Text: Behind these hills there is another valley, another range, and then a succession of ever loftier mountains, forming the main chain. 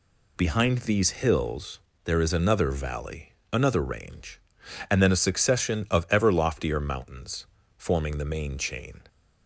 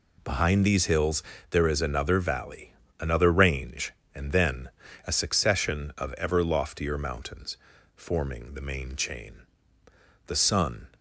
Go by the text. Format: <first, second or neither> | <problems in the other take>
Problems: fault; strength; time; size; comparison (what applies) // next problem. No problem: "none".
first | pauses between "hills" and "there"; slight; at 1.2 s; 0.28 s long; slight in the first // pauses between "then" and "a"; slight; at 4.6 s; 0.36 s long // goes on to say "The sun"; from 10.2 s on; 0.60 s long